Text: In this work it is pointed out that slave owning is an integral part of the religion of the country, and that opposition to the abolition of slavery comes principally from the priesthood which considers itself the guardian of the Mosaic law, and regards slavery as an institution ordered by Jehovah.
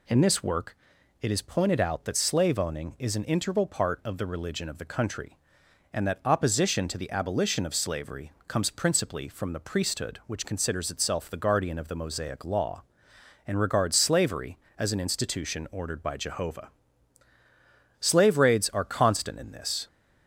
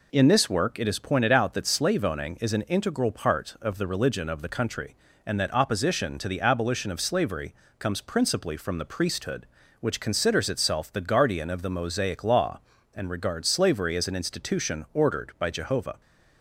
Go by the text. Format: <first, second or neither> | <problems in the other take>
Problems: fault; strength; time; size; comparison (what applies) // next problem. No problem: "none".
second | pauses between "work" and "it"; at 0.7 s; 0.44 s long // pauses between "slavery" and "comes"; slight; at 8.3 s; 0.16 s long; slight in the second // goes on to say "Slave raids are constant in this"; strong; from 18.0 s on; 1.8 s long